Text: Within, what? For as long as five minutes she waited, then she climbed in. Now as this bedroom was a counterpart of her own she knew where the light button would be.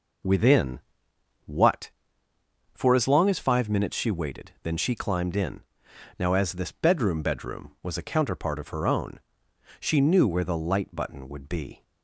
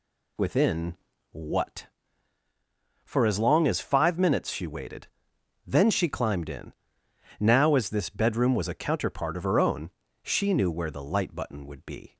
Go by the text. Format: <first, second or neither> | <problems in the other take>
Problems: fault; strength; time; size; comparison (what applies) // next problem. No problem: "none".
second | says "bedroom" twice; at 7.2 s // pauses between "own" and "she"; noticeable; at 9.1 s; 0.62 s long; slight in the second